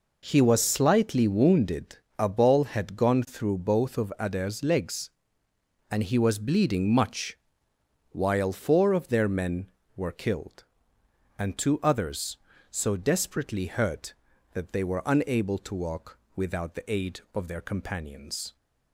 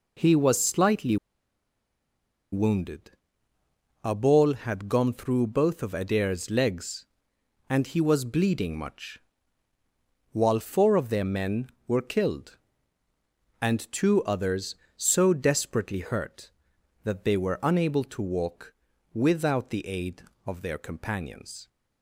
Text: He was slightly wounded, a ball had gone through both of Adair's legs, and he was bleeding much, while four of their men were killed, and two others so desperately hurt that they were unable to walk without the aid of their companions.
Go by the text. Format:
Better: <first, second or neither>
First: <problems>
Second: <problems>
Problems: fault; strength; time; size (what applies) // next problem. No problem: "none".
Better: first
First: pauses between "walk" and "without"; slight; at 16.1 s; 0.18 s long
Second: pauses between "slightly" and "wounded"; strong; at 1.1 s; 1.3 s long // pauses between "walk" and "without"; at 18.7 s; 0.40 s long